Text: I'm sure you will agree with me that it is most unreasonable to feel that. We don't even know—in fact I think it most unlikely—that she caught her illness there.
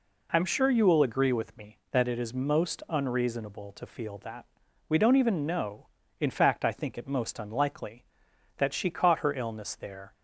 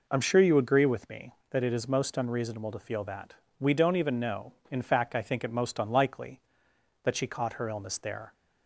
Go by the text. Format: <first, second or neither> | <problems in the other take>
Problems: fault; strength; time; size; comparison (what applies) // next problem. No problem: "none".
first | skips "will"; at 0.5 s